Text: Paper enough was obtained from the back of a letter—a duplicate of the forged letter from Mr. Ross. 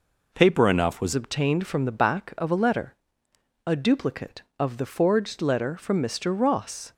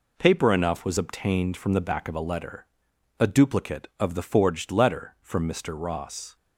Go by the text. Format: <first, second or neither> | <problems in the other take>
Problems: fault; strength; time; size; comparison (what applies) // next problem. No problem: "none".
second | changes voice at "obtained"; from 1.1 s on; 5.8 s long